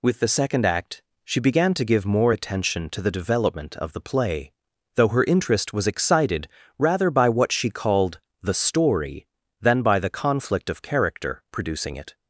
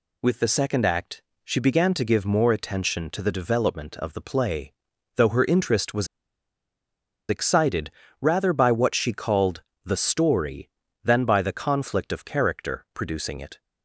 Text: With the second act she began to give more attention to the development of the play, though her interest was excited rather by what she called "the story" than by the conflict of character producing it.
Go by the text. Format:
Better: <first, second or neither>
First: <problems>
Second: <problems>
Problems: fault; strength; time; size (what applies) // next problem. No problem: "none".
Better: first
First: pauses between "act" and "she"; slight; at 1.0 s; 0.24 s long // pauses between "excited" and "rather"; slight; at 6.4 s; 0.32 s long // pauses between "called" and "the"; slight; at 8.2 s; 0.22 s long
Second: pauses between "act" and "she"; slight; at 1.2 s; 0.24 s long // pauses between "was" and "excited"; at 6.0 s; 1.2 s long // pauses between "excited" and "rather"; slight; at 7.8 s; 0.32 s long // pauses between "called" and "the"; slight; at 9.6 s; 0.22 s long